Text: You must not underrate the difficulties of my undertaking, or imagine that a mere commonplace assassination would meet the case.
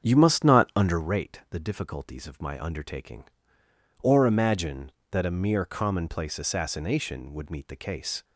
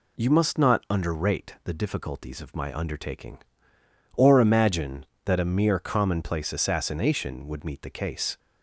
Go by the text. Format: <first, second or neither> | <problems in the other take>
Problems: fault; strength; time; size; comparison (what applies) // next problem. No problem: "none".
second | starts louder than the rest; strong; until 1.1 s; 7.5 dB